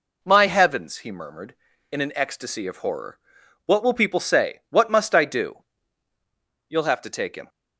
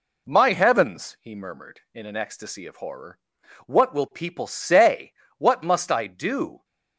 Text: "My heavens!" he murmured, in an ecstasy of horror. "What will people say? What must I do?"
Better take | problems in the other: second | goes on to say "You'll have to take him"; noticeable; from 6.6 s on; 0.80 s long

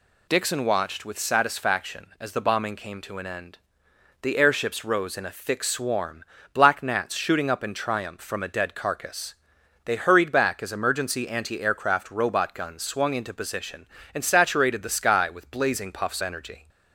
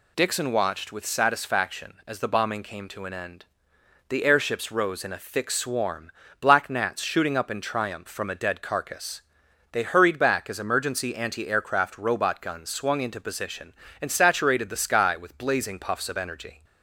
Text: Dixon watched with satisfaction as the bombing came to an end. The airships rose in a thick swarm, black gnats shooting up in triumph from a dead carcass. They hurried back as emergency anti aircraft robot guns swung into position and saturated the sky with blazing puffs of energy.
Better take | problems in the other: second | skips "of"; at 16.2 s

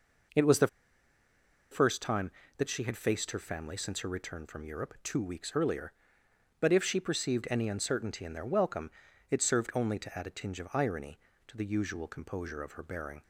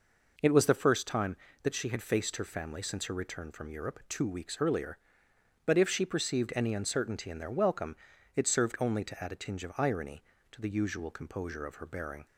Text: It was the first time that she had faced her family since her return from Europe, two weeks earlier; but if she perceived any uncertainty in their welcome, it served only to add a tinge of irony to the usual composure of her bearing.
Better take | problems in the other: second | pauses between "the" and "first"; at 0.6 s; 1.0 s long

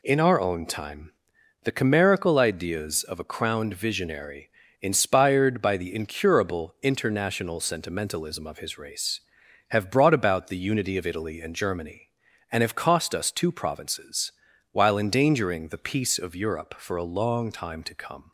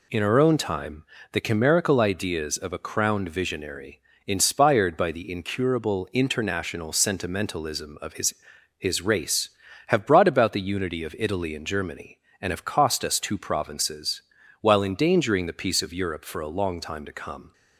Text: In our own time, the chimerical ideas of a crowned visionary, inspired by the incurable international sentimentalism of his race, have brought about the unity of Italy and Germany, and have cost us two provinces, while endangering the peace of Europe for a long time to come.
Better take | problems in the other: first | says "his" twice; at 8.7 s

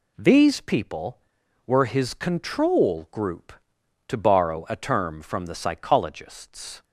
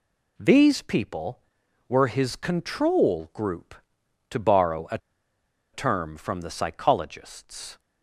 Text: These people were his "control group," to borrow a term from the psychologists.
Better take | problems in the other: first | pauses between "a" and "term"; noticeable; at 4.9 s; 0.75 s long

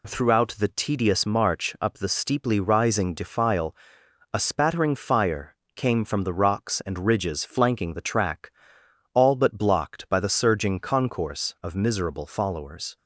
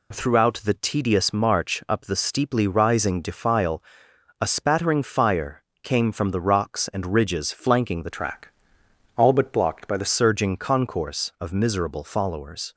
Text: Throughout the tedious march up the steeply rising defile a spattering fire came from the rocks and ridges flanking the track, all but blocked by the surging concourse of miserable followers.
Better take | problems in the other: first | pauses between "defile" and "a"; noticeable; at 3.8 s; 0.60 s long; noticeable in the first // pauses between "fire" and "came"; slight; at 5.6 s; 0.20 s long; slight in the first // changes voice from "track" to "the"; from 8.0 to 10.0 s; 2.0 s long

